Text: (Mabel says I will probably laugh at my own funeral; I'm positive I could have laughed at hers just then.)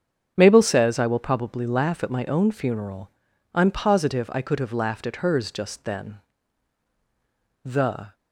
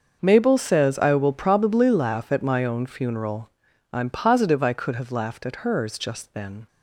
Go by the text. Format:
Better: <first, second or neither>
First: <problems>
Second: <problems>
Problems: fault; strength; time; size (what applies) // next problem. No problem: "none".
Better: second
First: starts louder than the rest; strong; until 1.3 s; 7.5 dB // goes on to say "The"; from 7.6 s on; 0.50 s long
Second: starts louder than the rest; until 1.2 s; 6 dB